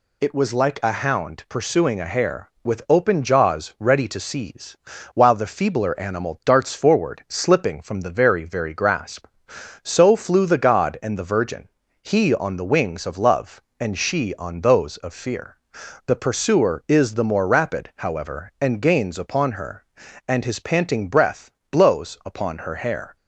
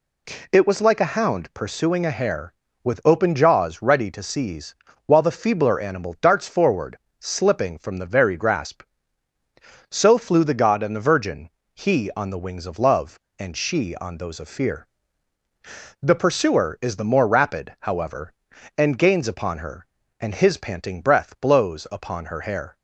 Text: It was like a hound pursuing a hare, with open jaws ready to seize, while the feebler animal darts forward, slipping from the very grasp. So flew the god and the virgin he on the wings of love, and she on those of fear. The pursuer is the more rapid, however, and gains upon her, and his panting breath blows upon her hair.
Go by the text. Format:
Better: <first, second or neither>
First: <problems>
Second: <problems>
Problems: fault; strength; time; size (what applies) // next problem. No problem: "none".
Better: second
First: says "very" twice; at 8.4 s // pauses between "virgin" and "he"; slight; at 11.6 s; 0.34 s long // pauses between "breath" and "blows"; slight; at 21.4 s; 0.22 s long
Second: pauses between "virgin" and "he"; slight; at 11.4 s; 0.24 s long